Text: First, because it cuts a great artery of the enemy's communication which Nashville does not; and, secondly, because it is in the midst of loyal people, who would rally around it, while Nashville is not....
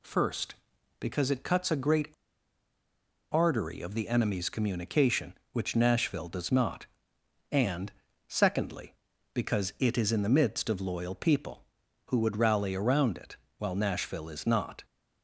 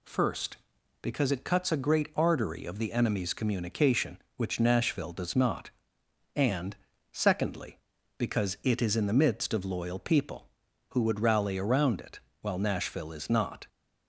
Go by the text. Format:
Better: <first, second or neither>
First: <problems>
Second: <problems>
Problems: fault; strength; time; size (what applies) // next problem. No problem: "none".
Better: second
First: pauses between "great" and "artery"; at 2.0 s; 1.2 s long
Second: none